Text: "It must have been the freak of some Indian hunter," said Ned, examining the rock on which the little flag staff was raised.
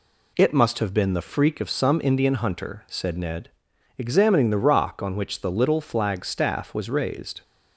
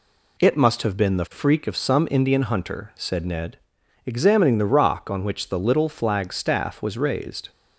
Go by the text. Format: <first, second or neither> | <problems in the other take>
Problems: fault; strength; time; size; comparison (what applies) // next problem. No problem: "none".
neither | none